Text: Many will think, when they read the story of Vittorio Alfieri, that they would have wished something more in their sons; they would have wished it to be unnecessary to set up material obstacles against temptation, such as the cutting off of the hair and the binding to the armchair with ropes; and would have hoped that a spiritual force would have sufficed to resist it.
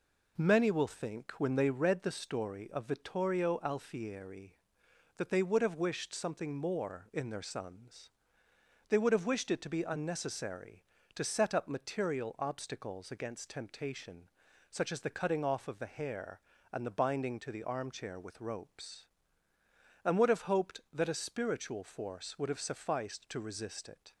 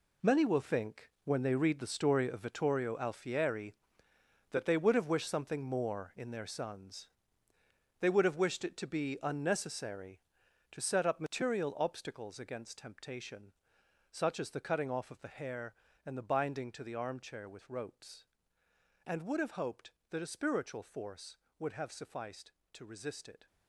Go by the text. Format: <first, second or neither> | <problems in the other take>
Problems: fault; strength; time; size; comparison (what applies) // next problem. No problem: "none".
first | gets quieter; strong; throughout; 11 dB